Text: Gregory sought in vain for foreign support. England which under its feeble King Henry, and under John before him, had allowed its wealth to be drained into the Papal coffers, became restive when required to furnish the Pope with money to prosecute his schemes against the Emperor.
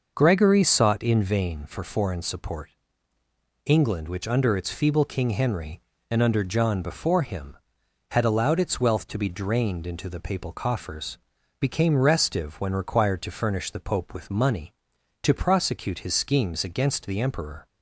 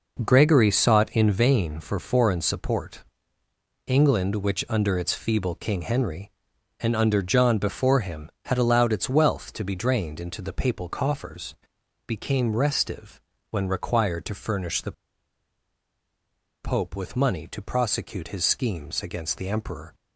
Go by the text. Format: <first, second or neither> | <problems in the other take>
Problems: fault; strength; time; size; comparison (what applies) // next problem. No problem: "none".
first | pauses between "restive" and "when"; slight; at 13.1 s; 0.32 s long // pauses between "the" and "Pope"; strong; at 14.9 s; 1.7 s long